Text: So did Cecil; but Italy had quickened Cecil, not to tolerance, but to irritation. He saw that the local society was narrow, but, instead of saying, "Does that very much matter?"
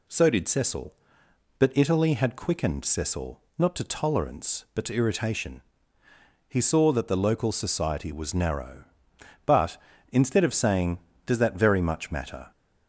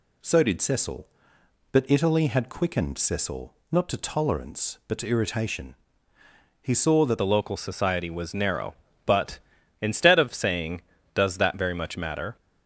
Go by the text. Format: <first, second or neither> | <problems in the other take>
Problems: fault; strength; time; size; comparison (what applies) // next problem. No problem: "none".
first | changes voice at "the"; from 7.1 s on; 5.2 s long